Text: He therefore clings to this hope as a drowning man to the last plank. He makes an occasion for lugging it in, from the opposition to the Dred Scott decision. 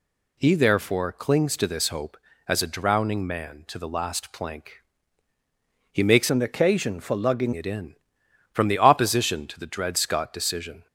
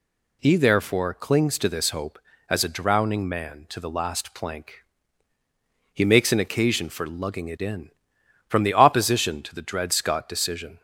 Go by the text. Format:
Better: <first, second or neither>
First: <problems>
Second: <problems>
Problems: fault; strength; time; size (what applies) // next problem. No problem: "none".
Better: second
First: changes voice from "an" to "lugging"; from 6.3 to 7.5 s; 1.2 s long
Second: none